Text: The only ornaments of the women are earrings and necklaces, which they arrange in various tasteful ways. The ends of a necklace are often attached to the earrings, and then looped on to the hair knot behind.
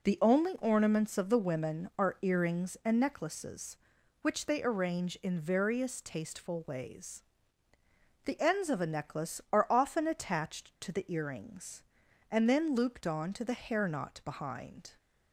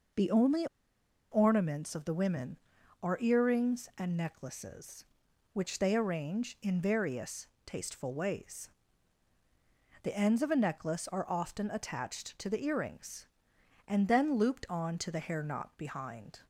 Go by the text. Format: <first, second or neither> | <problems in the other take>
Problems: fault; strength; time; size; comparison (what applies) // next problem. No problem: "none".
first | pauses between "only" and "ornaments"; noticeable; at 0.6 s; 0.64 s long // pauses between "various" and "tasteful"; slight; at 7.4 s; 0.16 s long